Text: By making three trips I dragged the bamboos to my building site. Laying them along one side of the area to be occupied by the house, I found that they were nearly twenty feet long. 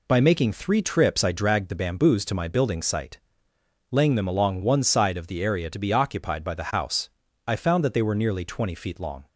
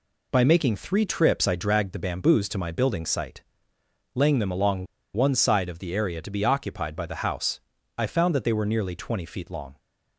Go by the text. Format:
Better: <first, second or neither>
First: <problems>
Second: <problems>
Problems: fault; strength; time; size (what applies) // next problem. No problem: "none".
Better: first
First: none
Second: pauses between "along" and "one"; slight; at 4.8 s; 0.28 s long